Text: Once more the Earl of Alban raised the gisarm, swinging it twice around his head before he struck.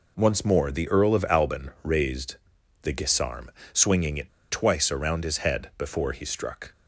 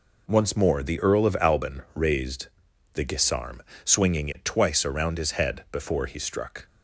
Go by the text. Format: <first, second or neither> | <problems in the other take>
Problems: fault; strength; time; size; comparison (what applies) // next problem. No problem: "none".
second | pauses between "raised" and "the"; noticeable; at 2.3 s; 0.46 s long; noticeable in the second // pauses between "it" and "twice"; slight; at 4.2 s; 0.19 s long